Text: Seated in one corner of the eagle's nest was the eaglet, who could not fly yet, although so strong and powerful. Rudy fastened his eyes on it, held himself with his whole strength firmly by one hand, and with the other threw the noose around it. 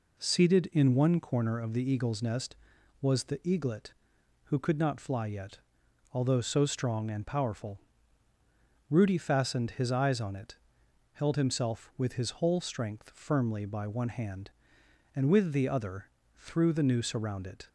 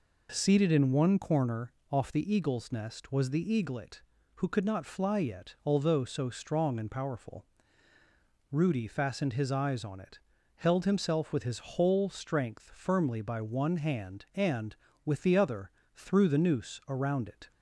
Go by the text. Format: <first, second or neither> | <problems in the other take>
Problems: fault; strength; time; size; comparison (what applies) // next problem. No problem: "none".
first | says "off" for "of"; at 1.9 s // pauses between "other" and "threw"; slight; at 15.7 s; 0.24 s long; slight in the first